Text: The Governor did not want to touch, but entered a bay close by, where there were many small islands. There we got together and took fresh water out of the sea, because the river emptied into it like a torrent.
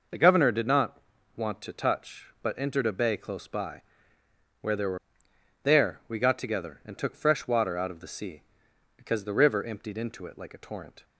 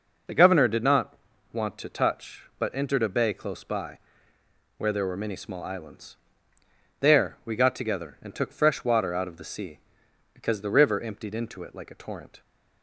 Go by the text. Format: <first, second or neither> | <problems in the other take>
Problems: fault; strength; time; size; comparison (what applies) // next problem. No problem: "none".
second | pauses between "not" and "want"; at 0.9 s; 0.38 s long; also in the second // skips "many small islands"; at 5.3 s